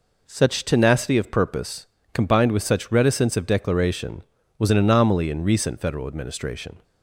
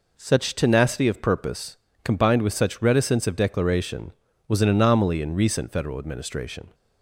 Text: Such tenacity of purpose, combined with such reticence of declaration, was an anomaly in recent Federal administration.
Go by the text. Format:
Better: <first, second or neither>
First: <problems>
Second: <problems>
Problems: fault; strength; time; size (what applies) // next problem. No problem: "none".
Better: neither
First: none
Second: none